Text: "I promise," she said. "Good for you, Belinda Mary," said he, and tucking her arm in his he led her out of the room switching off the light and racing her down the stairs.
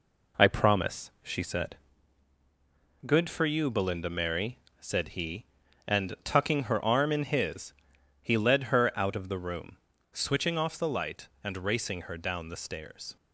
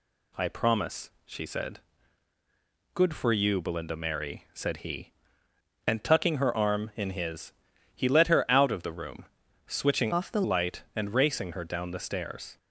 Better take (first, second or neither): first